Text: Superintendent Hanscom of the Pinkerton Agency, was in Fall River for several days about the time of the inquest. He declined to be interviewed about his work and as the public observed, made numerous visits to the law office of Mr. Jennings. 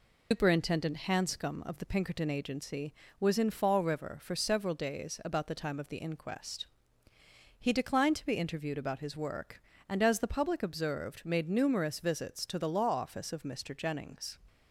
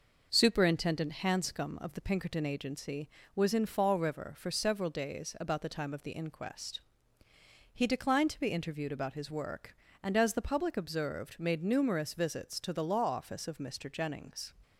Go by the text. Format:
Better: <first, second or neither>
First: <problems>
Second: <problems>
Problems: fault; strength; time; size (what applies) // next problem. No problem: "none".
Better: second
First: loses the start of "Superintendent"; at 0.3 s; 145 ms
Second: none